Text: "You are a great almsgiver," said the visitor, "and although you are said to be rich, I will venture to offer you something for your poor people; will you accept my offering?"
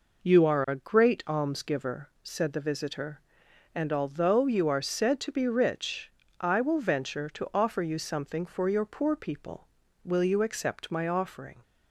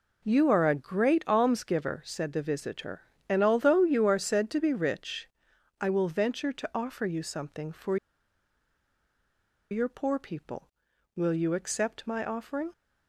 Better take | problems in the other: first | pauses between "for" and "your"; strong; at 7.9 s; 1.7 s long

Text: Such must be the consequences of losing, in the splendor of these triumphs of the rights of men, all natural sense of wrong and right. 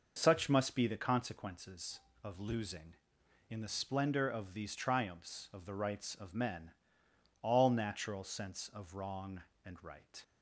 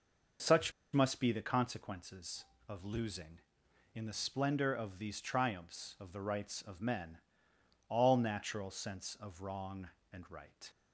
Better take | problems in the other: first | pauses between "Such" and "must"; slight; at 0.7 s; 0.22 s long

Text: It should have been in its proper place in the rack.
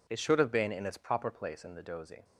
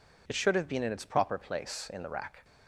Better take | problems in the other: second | says "dozy" for "rack"; at 1.8 s

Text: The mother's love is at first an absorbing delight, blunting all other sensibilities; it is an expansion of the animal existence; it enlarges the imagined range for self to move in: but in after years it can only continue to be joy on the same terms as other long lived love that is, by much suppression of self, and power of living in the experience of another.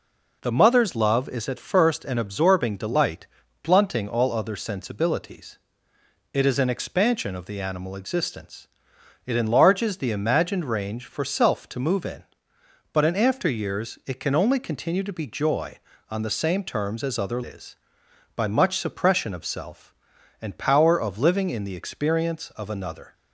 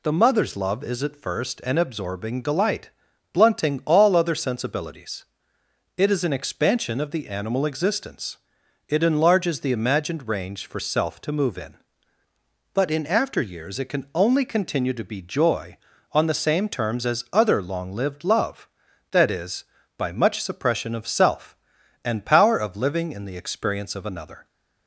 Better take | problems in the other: second | skips "long lived love that"; at 17.4 s

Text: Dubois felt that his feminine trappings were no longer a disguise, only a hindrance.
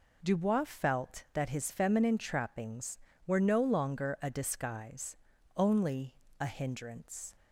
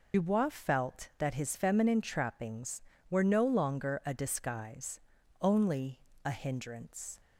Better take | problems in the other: first | loses the start of "Dubois"; at 0.1 s; 65 ms // pauses between "only" and "a"; slight; at 6.0 s; 0.24 s long; slight in the first

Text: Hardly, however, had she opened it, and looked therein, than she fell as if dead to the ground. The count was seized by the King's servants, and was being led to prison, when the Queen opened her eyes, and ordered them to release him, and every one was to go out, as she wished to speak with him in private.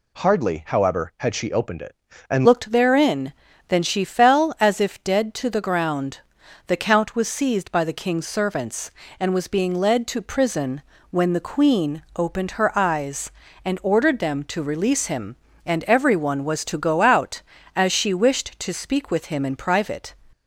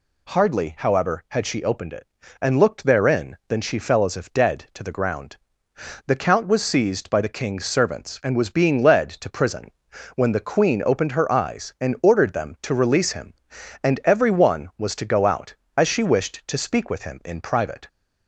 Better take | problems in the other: second | changes voice at "looked"; from 2.4 s on; 17.7 s long

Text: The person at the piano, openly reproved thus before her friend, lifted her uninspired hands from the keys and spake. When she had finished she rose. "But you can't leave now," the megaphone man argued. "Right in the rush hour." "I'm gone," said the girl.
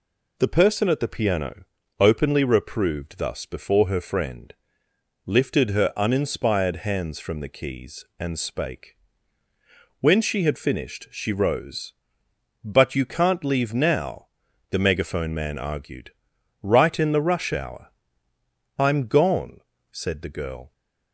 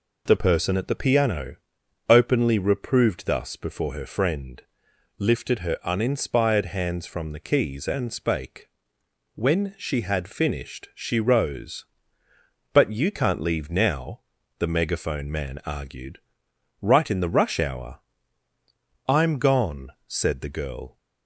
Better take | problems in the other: neither | none

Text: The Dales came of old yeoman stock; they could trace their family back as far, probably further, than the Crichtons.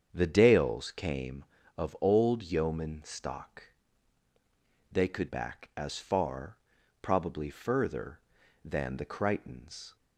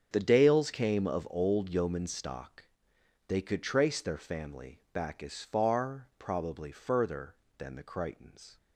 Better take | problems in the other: second | starts louder than the rest; strong; until 1.1 s; 7.5 dB; strong in the second // skips "trace their family"; at 5.2 s

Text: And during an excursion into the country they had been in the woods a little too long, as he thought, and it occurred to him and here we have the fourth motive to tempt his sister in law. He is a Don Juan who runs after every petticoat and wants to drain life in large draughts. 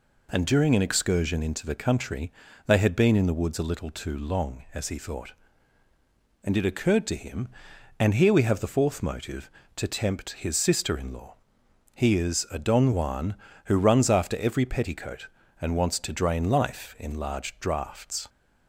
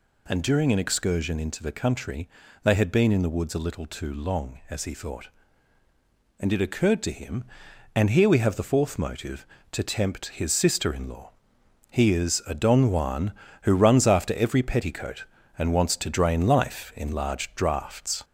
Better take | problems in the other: first | gets louder; slight; throughout; 3 dB // pauses between "country" and "they"; slight; at 2.2 s; 0.34 s long; slight in the first

